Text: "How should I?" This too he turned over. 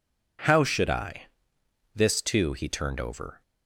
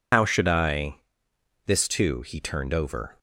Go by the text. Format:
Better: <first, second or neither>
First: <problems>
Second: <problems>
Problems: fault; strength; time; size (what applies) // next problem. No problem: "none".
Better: first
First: none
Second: loses the start of "How"; at 0.1 s; 100 ms